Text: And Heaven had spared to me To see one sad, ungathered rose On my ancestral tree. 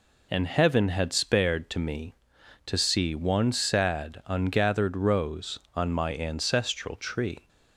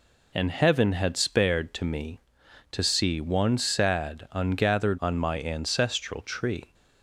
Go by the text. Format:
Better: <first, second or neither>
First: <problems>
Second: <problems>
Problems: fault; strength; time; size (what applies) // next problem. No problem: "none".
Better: first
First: none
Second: skips "rose"; at 4.9 s